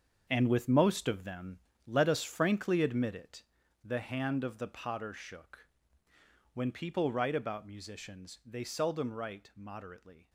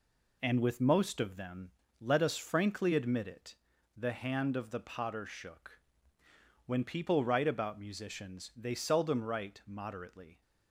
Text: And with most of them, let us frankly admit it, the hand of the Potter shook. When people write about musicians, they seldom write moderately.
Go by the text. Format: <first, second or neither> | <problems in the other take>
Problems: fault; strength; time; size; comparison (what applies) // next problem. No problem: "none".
second | gets quieter; strong; throughout; 12 dB